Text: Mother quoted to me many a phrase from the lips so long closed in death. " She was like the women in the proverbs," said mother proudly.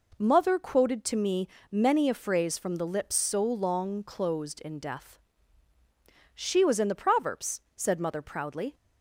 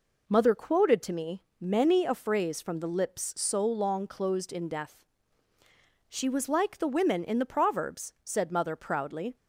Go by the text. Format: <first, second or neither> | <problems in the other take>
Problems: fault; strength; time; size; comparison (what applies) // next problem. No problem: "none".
second | pauses between "me" and "many"; slight; at 1.4 s; 0.24 s long; slight in the second // skips "like the women"; at 6.7 s